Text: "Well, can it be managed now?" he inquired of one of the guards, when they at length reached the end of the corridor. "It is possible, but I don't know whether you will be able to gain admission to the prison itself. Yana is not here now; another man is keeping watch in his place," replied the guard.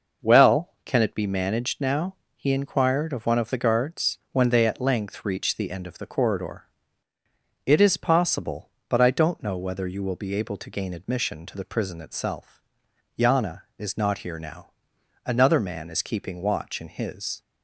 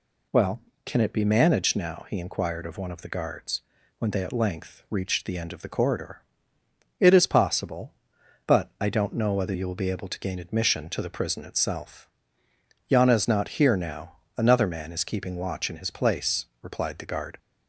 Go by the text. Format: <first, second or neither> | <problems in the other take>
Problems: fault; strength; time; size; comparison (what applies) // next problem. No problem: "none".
second | stops before "place replied the guard"; at 17.4 s